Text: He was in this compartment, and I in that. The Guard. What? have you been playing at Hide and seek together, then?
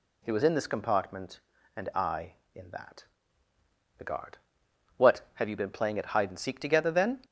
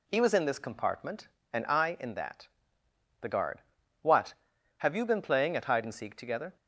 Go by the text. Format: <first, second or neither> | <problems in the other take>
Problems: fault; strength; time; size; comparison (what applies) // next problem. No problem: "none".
first | stops before "then"; at 6.5 s